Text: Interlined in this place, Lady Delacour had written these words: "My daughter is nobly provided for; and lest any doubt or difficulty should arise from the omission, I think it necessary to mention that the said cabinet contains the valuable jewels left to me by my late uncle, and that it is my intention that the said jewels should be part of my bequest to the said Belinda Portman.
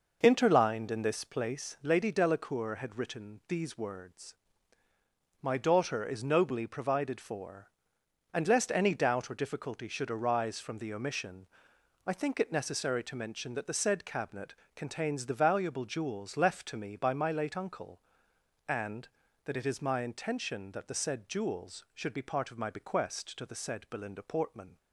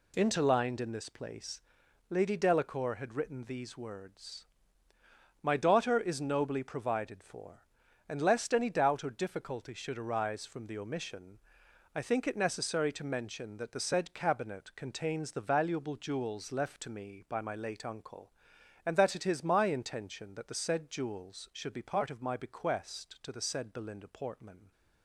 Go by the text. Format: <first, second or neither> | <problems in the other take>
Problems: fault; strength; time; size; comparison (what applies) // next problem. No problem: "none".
second | starts louder than the rest; noticeable; until 1.7 s; 5.5 dB // pauses between "cabinet" and "contains"; slight; at 14.5 s; 0.22 s long